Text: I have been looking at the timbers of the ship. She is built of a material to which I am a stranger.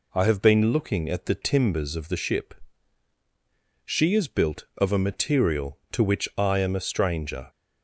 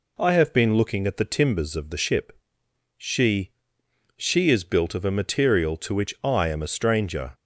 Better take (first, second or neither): first